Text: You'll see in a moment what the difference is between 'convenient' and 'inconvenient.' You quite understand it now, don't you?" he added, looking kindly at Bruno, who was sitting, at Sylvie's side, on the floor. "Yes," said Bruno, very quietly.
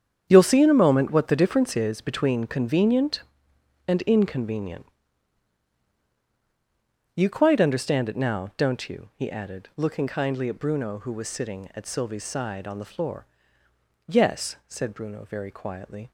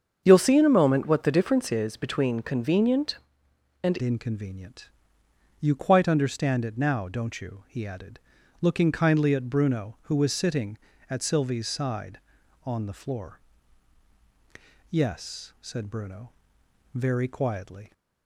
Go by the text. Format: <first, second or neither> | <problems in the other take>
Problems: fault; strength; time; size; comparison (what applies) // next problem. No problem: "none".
first | starts louder than the rest; strong; until 1.2 s; 7.5 dB; strong in the first // changes voice at "inconvenient"; from 4.0 s on; 13.9 s long